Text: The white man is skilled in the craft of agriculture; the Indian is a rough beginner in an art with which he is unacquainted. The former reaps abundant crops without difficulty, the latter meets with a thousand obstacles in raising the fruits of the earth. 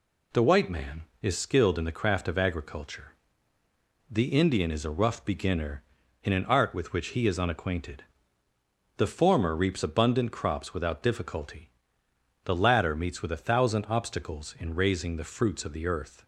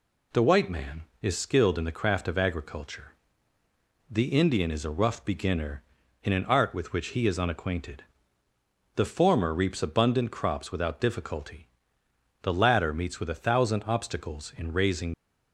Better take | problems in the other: first | stops before "the fruits of the earth"; at 15.1 s

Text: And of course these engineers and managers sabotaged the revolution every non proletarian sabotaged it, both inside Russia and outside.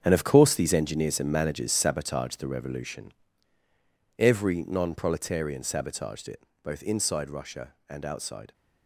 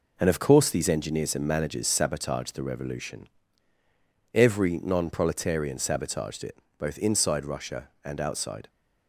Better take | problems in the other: second | gets quieter; strong; throughout; 12 dB // pauses between "revolution" and "every"; at 3.1 s; 1.0 s long; also in the second

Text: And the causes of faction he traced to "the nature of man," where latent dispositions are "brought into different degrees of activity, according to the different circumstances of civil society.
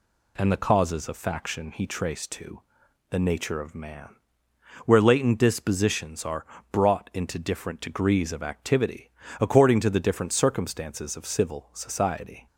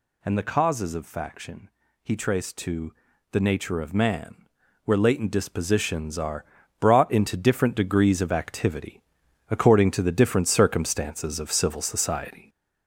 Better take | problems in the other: first | gets louder; noticeable; throughout; 5.5 dB // pauses between "faction" and "he"; slight; at 1.6 s; 0.34 s long // pauses between "to" and "the"; at 2.9 s; 0.38 s long; noticeable in the first // pauses between "are" and "brought"; slight; at 6.4 s; 0.34 s long; slight in the first

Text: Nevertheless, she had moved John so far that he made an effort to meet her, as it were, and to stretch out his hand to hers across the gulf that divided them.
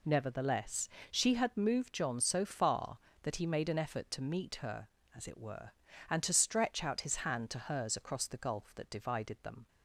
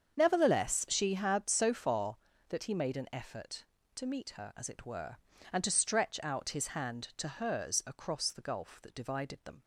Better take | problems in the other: first | starts louder than the rest; strong; until 1.2 s; 7 dB // skips "moved John"; at 1.4 s

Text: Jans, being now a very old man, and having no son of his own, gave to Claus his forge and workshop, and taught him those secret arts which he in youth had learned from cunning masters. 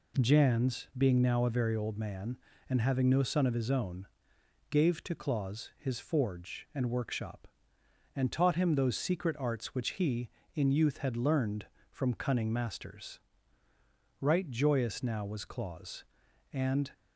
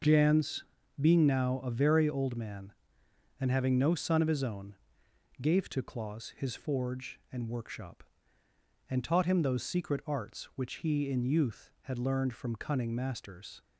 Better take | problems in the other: second | goes on to say "Right joyous now was Claus and"; strong; from 14.1 s on; 2.7 s long

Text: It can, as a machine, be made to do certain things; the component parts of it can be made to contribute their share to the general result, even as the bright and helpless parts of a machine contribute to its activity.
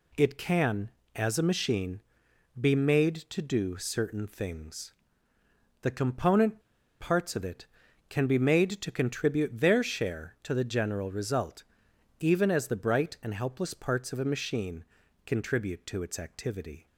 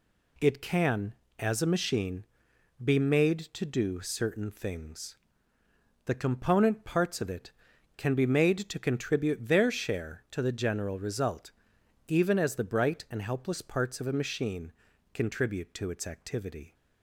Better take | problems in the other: second | pauses between "component" and "parts"; at 6.5 s; 0.40 s long // pauses between "machine" and "contribute"; at 14.8 s; 0.40 s long; also in the second

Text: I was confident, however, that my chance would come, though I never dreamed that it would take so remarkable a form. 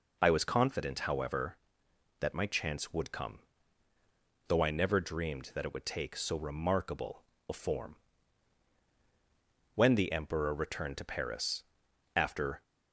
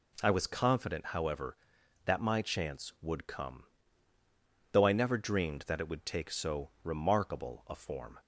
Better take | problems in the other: second | pauses between "remarkable" and "a"; slight; at 7.2 s; 0.26 s long // goes on to say "When the Emperor returned to Paris after"; strong; from 9.7 s on; 2.8 s long

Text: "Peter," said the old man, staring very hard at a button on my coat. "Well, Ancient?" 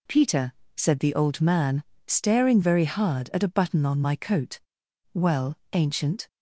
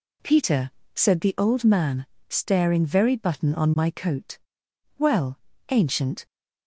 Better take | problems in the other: first | skips "hard at a"; at 3.1 s

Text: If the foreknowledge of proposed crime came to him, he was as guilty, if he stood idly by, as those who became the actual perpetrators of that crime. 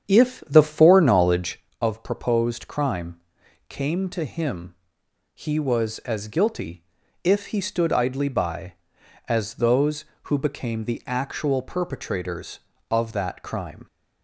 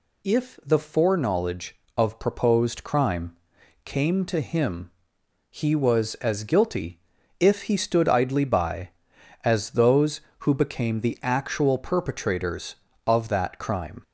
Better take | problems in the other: second | starts louder than the rest; strong; until 1.8 s; 8.5 dB // pauses between "crime" and "came"; noticeable; at 3.2 s; 0.48 s long; noticeable in the second

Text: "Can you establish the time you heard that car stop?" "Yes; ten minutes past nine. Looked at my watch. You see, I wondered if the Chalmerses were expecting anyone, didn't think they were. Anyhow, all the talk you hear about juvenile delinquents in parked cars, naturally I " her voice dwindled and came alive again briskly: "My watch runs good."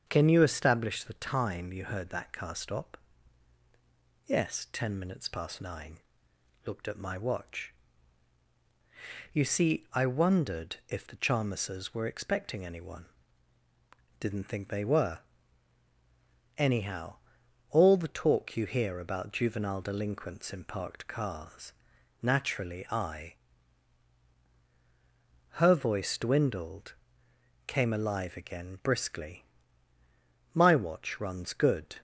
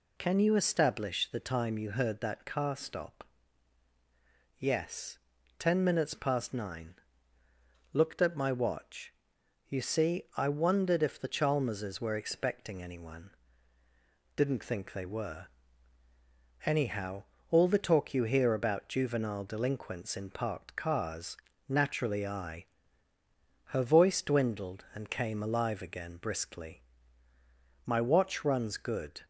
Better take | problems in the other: second | starts louder than the rest; until 1.0 s; 7 dB // skips "and"; at 27.3 s

